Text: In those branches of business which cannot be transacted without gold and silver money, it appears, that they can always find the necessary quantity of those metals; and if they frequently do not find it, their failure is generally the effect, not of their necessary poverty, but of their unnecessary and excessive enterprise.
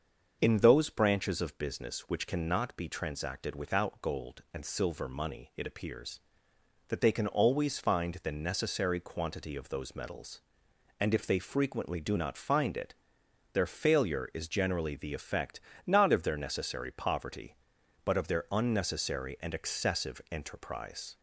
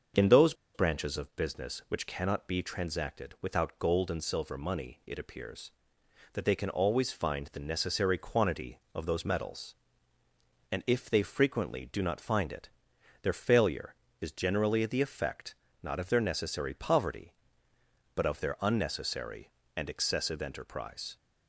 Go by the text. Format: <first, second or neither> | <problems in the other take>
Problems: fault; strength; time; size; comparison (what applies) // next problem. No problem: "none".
first | starts louder than the rest; until 1.3 s; 6.5 dB; also in the first // pauses between "those" and "branches"; slight; at 0.5 s; 0.21 s long